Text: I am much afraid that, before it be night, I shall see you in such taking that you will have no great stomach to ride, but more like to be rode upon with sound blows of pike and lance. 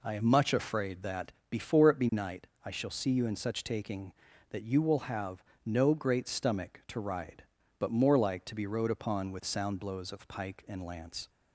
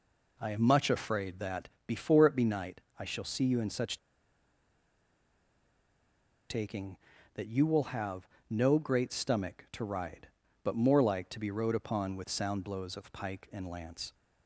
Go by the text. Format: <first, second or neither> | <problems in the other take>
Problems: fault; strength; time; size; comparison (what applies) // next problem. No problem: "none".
first | pauses between "such" and "taking"; strong; at 3.9 s; 2.5 s long // pauses between "have" and "no"; slight; at 8.2 s; 0.24 s long; slight in the first